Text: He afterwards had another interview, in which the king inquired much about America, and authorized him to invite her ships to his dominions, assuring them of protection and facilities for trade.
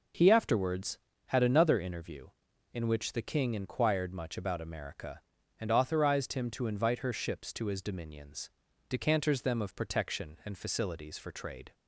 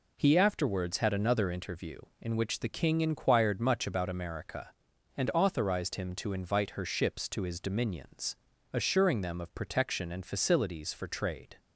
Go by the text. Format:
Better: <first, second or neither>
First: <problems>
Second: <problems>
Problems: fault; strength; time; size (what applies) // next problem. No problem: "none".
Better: second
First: says "decanters" for "assuring"; at 8.8 s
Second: none